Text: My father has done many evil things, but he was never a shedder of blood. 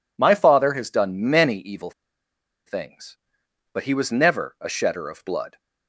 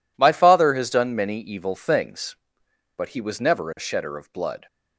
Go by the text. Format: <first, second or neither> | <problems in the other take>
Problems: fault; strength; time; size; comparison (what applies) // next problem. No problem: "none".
second | pauses between "evil" and "things"; noticeable; at 1.9 s; 0.75 s long